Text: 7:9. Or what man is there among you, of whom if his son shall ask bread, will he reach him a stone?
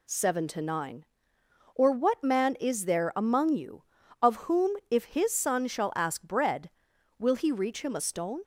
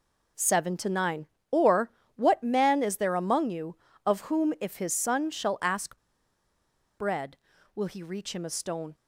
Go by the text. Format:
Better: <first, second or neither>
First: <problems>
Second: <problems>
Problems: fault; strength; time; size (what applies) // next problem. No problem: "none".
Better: first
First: none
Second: pauses between "Or" and "what"; slight; at 1.8 s; 0.28 s long // pauses between "ask" and "bread"; at 5.9 s; 1.0 s long